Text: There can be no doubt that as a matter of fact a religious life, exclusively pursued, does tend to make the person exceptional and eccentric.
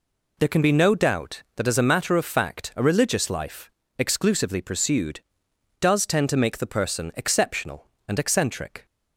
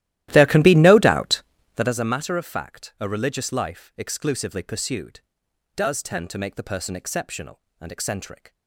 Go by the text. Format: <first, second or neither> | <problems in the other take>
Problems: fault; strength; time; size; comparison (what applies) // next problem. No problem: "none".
first | starts louder than the rest; strong; until 2.0 s; 14.5 dB